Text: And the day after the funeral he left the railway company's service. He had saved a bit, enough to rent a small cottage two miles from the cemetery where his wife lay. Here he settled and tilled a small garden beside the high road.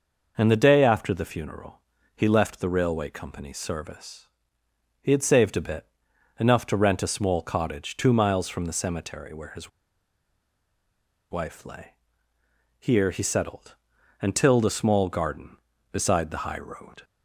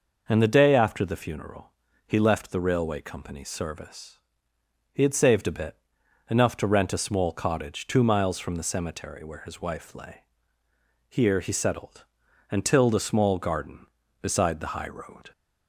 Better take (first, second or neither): second